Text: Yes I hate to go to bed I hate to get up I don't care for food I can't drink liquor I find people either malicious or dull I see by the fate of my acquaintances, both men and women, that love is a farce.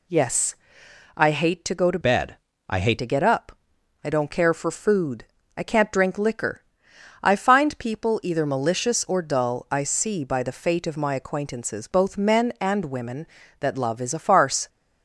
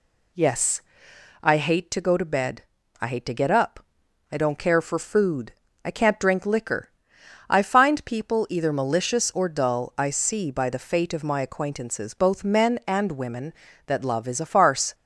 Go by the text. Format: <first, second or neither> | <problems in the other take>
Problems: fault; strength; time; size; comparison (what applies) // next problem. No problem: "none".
second | pauses between "Yes" and "I"; noticeable; at 0.5 s; 0.60 s long; noticeable in the second // changes voice from "bed" to "hate"; from 2.0 to 2.9 s; 0.9 s long // pauses between "bed" and "I"; slight; at 2.3 s; 0.32 s long; also in the second // pauses between "up" and "I"; noticeable; at 3.5 s; 0.52 s long; noticeable in the second // pauses between "food" and "I"; slight; at 5.2 s; 0.32 s long; slight in the second // pauses between "liquor" and "I"; noticeable; at 6.6 s; 0.60 s long; noticeable in the second